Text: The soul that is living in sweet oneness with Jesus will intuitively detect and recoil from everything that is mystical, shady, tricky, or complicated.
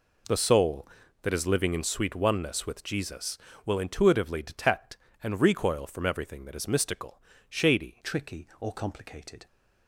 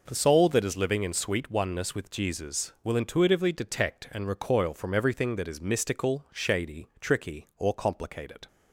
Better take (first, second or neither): second